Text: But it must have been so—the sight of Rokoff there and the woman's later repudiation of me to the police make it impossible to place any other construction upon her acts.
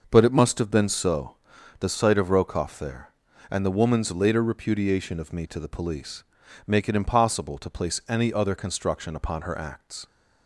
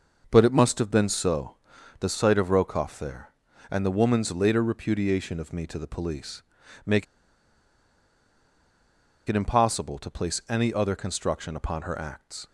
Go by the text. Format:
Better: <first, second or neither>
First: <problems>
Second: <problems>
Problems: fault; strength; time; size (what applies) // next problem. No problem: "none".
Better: first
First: pauses between "police" and "make"; at 6.2 s; 0.42 s long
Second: pauses between "police" and "make"; at 6.4 s; 0.42 s long // pauses between "make" and "it"; strong; at 7.0 s; 2.2 s long